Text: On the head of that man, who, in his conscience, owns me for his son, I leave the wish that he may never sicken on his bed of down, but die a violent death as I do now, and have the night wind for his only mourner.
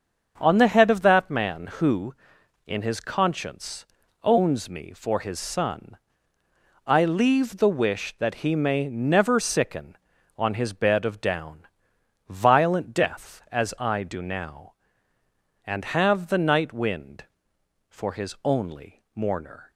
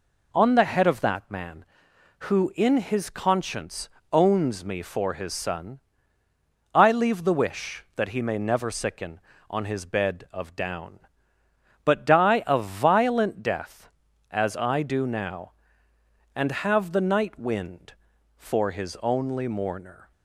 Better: second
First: starts louder than the rest; strong; until 1.3 s; 7 dB // skips "but die a"; at 11.9 s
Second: none

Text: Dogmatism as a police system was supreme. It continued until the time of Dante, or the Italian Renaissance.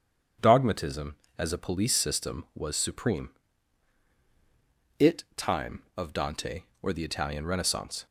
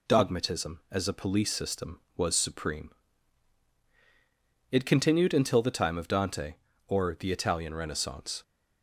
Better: second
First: starts louder than the rest; strong; until 1.6 s; 7.5 dB // skips "continued until the"; at 5.3 s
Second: none

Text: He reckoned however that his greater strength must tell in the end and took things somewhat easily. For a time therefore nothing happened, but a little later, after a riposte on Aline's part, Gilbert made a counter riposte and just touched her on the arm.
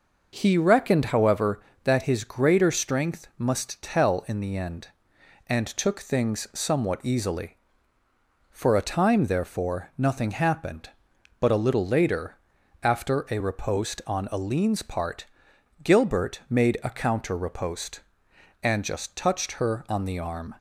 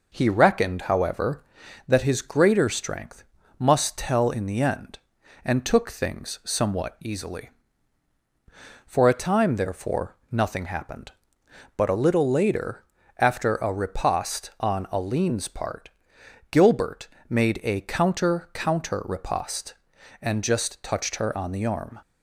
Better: first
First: none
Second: pauses between "strength" and "must"; slight; at 3.2 s; 0.34 s long // pauses between "Gilbert" and "made"; slight; at 17.0 s; 0.22 s long // says "counter" twice; at 18.5 s

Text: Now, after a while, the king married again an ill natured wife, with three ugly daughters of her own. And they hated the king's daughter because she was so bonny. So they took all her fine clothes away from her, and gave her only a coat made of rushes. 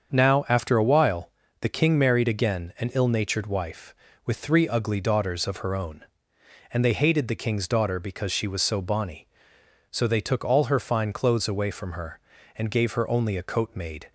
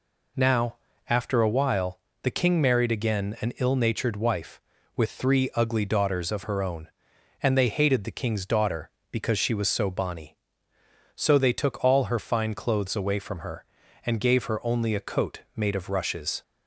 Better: second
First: starts louder than the rest; until 1.1 s; 7 dB // stops before "of rushes"; at 14.0 s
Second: none

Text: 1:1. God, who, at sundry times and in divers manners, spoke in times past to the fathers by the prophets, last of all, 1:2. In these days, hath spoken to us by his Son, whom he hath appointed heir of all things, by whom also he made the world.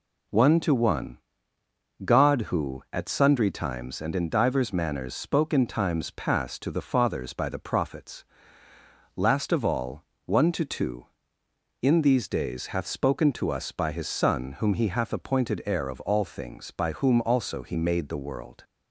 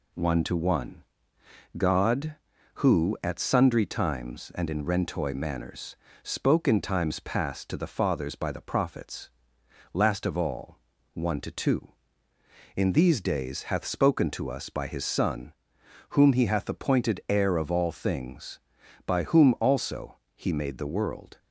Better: first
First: none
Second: says "rentoy" for "divers"; at 4.8 s // pauses between "also" and "he"; slight; at 20.1 s; 0.18 s long

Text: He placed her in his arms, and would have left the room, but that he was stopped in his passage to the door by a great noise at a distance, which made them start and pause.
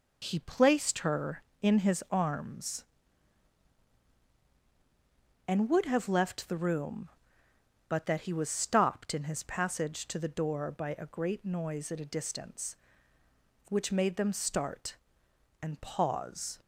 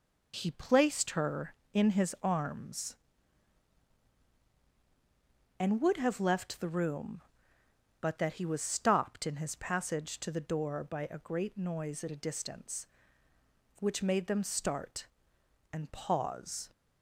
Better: neither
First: none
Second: none

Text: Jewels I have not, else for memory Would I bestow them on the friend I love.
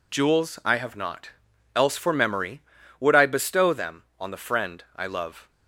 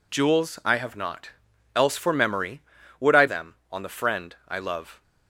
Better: first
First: none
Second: skips "bestow"; at 3.2 s

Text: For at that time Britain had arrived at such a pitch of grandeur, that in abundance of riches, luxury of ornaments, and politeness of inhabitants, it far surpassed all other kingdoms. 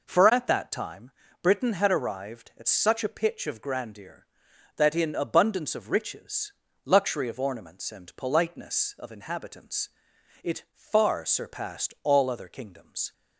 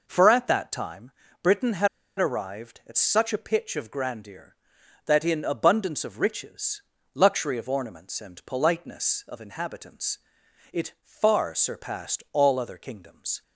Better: first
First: pauses between "time" and "Britain"; slight; at 1.1 s; 0.32 s long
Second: pauses between "time" and "Britain"; slight; at 1.1 s; 0.32 s long // pauses between "had" and "arrived"; slight; at 1.8 s; 0.31 s long

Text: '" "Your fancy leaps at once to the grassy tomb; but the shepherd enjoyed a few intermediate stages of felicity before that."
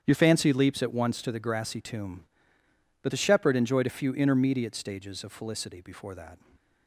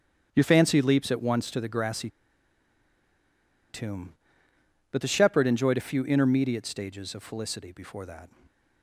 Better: first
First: starts louder than the rest; strong; until 1.0 s; 9 dB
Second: starts louder than the rest; strong; until 1.3 s; 9 dB // pauses between "grassy" and "tomb"; strong; at 2.0 s; 1.6 s long

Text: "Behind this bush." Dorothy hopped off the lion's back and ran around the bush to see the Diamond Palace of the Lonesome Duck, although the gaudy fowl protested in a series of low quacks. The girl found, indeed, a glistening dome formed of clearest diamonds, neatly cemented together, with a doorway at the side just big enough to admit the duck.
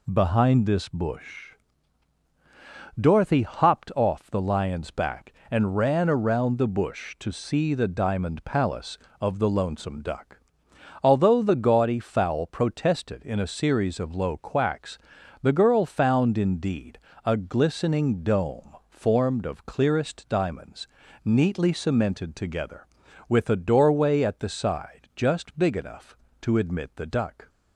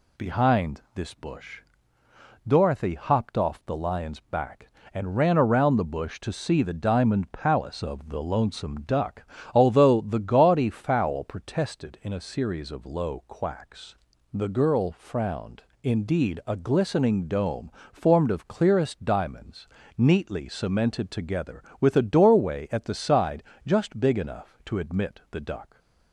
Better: first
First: none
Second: says "frowned" for "found"; at 14.9 s // pauses between "dome" and "formed"; slight; at 17.7 s; 0.24 s long // pauses between "side" and "just"; slight; at 23.4 s; 0.22 s long

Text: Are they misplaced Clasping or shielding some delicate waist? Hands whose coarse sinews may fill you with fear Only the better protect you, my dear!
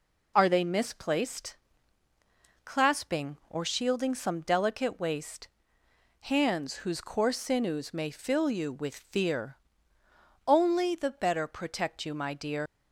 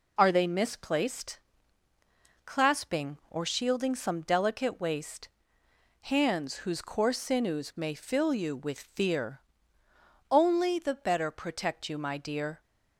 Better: second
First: pauses between "misplaced" and "Clasping"; at 1.5 s; 1.1 s long // pauses between "fear" and "Only"; noticeable; at 9.5 s; 0.90 s long // leaves "dear" unfinished; at 12.6 s; 100 ms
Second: pauses between "misplaced" and "Clasping"; at 1.3 s; 1.0 s long // pauses between "fear" and "Only"; noticeable; at 9.3 s; 0.90 s long

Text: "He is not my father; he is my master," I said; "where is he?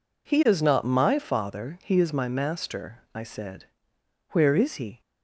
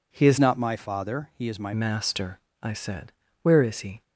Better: first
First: none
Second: changes voice from "not" to "my"; from 0.3 to 1.7 s; 1.4 s long

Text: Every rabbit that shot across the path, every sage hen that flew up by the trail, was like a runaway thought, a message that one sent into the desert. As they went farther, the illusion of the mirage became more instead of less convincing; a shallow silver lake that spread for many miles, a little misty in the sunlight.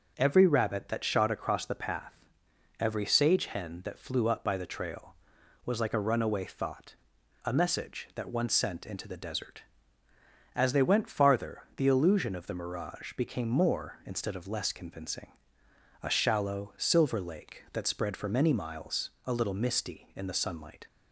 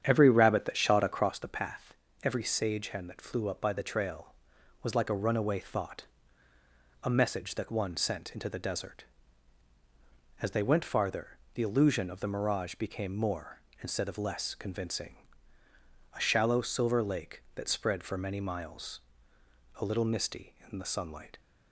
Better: first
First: none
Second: starts louder than the rest; strong; until 1.4 s; 8.5 dB

